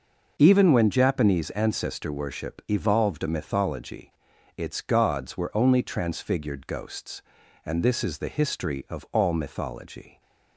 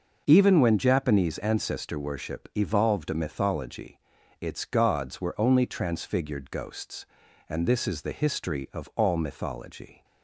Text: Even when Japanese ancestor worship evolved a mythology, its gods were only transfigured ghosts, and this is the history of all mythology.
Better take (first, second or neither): neither